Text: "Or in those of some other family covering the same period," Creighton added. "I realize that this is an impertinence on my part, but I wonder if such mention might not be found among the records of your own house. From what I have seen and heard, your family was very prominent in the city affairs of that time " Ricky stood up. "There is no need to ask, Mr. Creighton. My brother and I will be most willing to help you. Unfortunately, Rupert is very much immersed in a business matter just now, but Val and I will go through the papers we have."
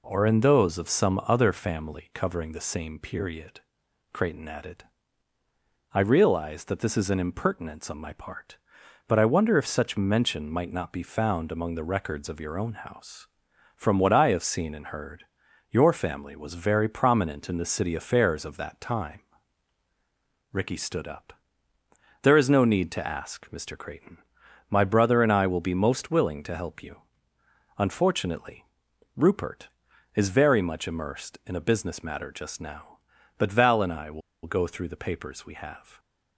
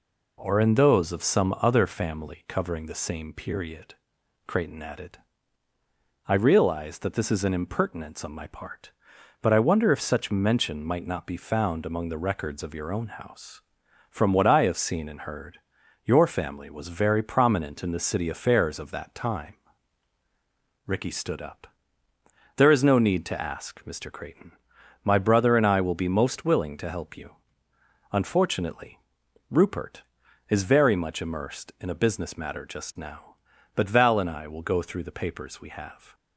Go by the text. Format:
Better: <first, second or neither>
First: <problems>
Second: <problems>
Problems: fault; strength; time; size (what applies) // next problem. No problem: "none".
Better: second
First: pauses between "will" and "go"; slight; at 34.2 s; 0.24 s long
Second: none